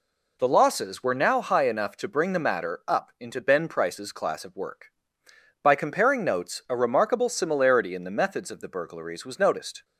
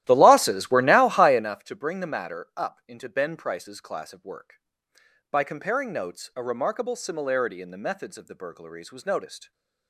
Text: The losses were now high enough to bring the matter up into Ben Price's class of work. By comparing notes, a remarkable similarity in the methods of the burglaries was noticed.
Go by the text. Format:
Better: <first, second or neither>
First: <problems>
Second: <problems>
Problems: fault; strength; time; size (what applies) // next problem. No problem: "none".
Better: first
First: none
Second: starts louder than the rest; strong; until 1.5 s; 14.5 dB